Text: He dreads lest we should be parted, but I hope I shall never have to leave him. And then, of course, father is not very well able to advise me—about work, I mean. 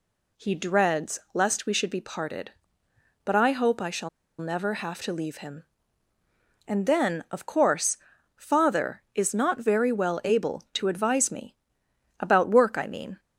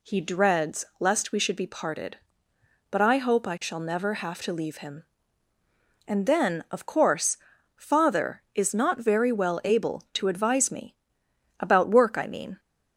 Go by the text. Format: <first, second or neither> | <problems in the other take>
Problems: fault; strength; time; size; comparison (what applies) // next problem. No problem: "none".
second | pauses between "dreads" and "lest"; slight; at 1.1 s; 0.16 s long; slight in the second // pauses between "shall" and "never"; slight; at 4.0 s; 0.30 s long